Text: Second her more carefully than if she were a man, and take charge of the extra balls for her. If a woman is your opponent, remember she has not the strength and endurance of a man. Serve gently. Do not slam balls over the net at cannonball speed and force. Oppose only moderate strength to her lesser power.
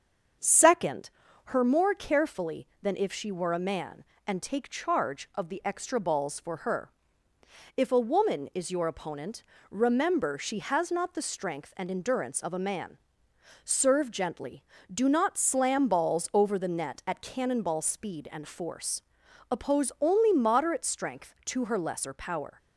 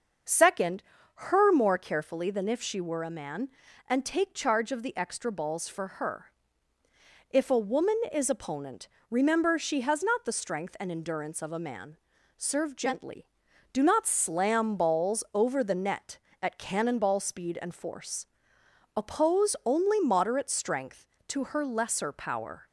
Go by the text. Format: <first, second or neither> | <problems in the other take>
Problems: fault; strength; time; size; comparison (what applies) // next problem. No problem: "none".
first | starts louder than the rest; until 1.5 s; 6.5 dB; also in the first // pauses between "Second" and "her"; slight; at 0.8 s; 0.34 s long; slight in the first // skips "your"; at 8.2 s